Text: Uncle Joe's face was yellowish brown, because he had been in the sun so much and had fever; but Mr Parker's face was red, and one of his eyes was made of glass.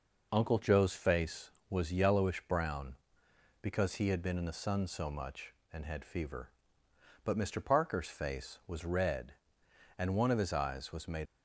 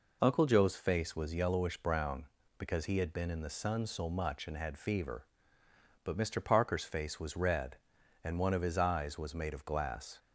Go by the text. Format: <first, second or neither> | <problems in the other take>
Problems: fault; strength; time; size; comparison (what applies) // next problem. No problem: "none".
second | stops before "of glass"; at 11.2 s